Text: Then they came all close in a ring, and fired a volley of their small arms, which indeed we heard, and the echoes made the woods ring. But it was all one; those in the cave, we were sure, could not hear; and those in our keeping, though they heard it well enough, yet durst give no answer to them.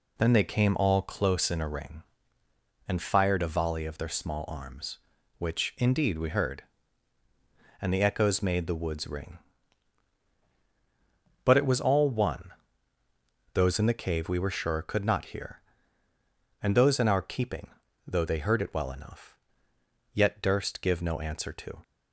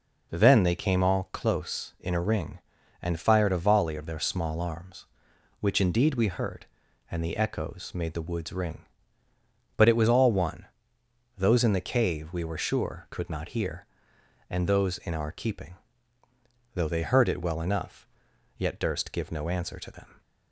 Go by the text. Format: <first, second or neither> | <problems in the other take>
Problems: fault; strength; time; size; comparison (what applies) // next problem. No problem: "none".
second | stops before "them"; at 21.8 s